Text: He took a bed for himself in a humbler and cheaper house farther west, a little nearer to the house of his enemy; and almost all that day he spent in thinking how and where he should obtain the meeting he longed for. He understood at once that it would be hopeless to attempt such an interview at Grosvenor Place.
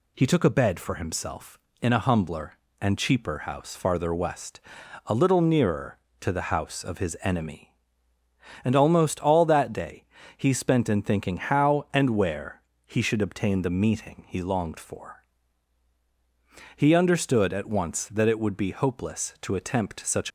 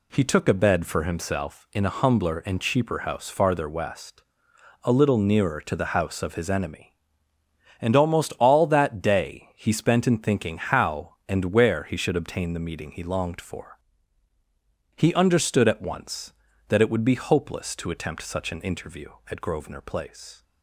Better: second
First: pauses between "day" and "he"; slight; at 10.0 s; 0.32 s long // pauses between "where" and "he"; slight; at 12.6 s; 0.24 s long // stops before "an interview at Grosvenor Place"; at 20.2 s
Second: none

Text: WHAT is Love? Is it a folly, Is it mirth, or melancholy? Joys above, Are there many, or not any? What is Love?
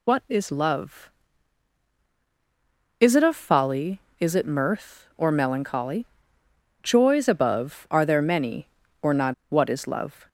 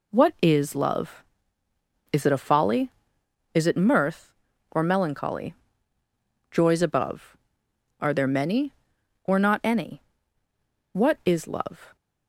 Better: second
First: skips "any"; at 9.4 s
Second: none

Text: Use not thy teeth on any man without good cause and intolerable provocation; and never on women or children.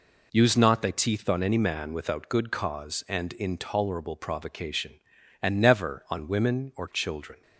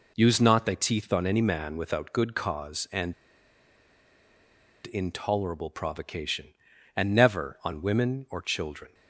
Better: first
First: none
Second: pauses between "and" and "intolerable"; strong; at 3.1 s; 1.7 s long

